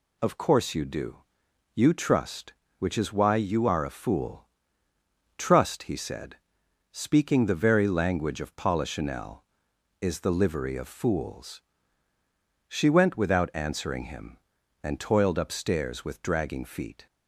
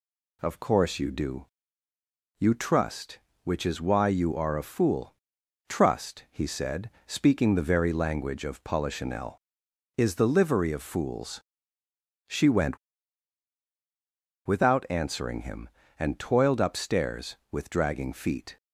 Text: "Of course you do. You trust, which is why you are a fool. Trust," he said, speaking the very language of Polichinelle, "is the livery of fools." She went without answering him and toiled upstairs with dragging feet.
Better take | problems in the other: first | pauses between "went" and "without"; strong; at 12.7 s; 1.6 s long

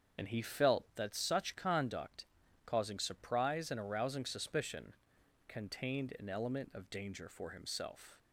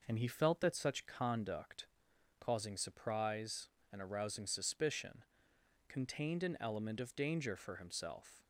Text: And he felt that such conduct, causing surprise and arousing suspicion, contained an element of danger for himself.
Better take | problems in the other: second | loses the start of "And"; at 0.1 s; 40 ms // starts louder than the rest; strong; until 1.2 s; 7 dB

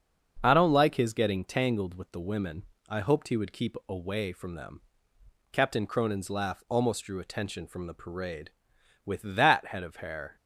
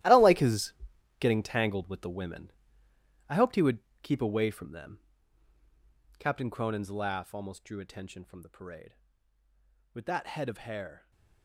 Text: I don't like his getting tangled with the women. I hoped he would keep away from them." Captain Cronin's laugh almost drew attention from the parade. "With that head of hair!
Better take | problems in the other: first | gets quieter; strong; throughout; 15 dB // starts louder than the rest; strong; until 1.4 s; 14.5 dB; also in the first // pauses between "his" and "getting"; noticeable; at 0.7 s; 0.46 s long // pauses between "would" and "keep"; slight; at 3.7 s; 0.22 s long

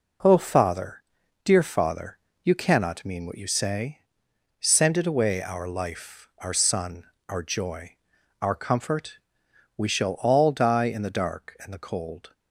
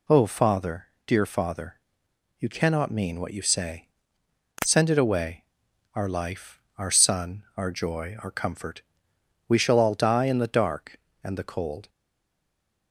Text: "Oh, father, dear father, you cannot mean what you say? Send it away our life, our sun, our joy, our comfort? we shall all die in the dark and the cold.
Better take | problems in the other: first | pauses between "away" and "our"; noticeable; at 5.4 s; 0.50 s long // stays silent after the last word; from 11.8 s on; 1.1 s long

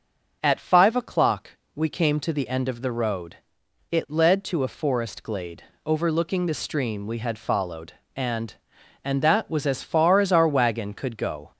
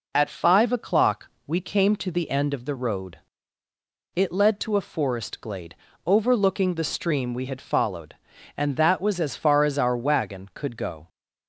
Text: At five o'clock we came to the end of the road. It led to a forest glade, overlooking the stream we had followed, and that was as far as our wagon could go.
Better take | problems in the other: second | pauses between "o'clock" and "we"; slight; at 1.4 s; 0.24 s long; slight in the second // says "and" twice; at 9.0 s

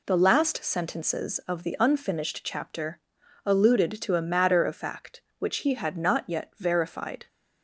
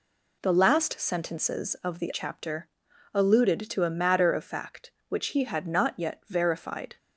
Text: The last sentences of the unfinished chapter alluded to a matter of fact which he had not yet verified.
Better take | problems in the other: first | skips "unfinished"; at 2.1 s // pauses between "chapter" and "alluded"; noticeable; at 2.6 s; 0.46 s long; noticeable in the first

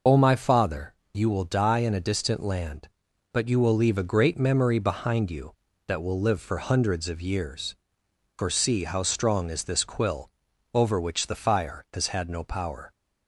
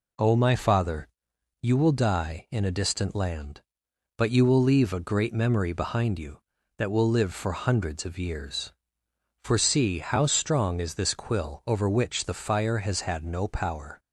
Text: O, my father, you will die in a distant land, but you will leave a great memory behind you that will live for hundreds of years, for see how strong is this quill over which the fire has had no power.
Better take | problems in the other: second | loses the start of "O"; at 0.0 s; 60 ms // pauses between "quill" and "over"; at 10.2 s; 0.42 s long

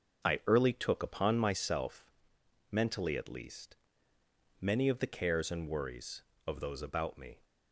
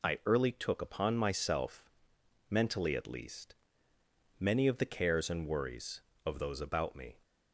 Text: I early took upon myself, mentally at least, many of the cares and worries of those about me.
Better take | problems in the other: second | starts louder than the rest; until 1.6 s; 6.5 dB

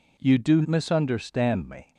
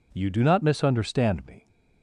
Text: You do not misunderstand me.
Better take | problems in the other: second | skips "not"; at 0.6 s

